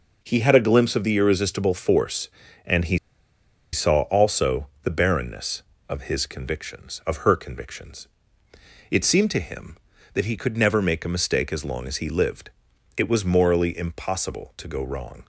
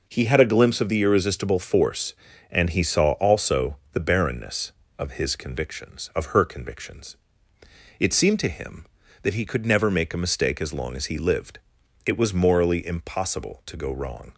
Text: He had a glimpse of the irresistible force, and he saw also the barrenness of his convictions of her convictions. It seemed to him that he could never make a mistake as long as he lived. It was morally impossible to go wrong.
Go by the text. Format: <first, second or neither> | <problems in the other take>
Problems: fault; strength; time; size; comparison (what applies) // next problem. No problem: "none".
second | pauses between "he" and "saw"; noticeable; at 2.9 s; 0.75 s long // pauses between "also" and "the"; slight; at 4.6 s; 0.18 s long; slight in the second